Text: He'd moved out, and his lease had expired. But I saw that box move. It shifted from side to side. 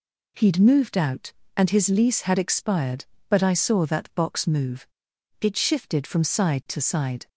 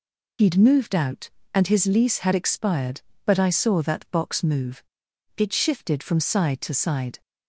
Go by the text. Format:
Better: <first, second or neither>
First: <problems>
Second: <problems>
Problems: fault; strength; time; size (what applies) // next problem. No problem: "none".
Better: first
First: none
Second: loses the start of "He'd"; at 0.3 s; 45 ms